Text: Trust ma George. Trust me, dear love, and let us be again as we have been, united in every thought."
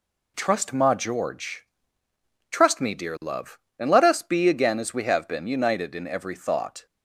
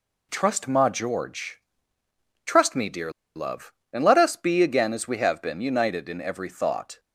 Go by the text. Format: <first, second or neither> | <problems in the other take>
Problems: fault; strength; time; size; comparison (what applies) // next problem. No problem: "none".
first | pauses between "dear" and "love"; slight; at 3.1 s; 0.23 s long